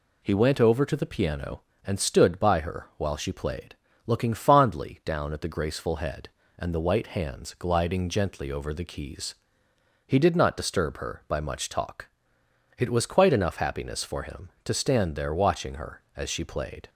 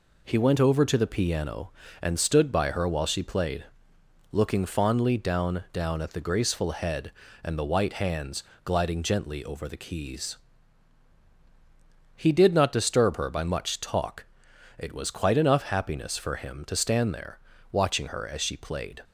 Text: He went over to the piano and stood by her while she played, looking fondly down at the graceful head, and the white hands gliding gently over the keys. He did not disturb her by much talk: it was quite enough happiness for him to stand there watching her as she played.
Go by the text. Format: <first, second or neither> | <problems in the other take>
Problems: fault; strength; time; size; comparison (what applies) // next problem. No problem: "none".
first | says "down" twice; at 5.7 s // pauses between "hands" and "gliding"; slight; at 8.4 s; 0.22 s long // pauses between "there" and "watching"; slight; at 17.3 s; 0.34 s long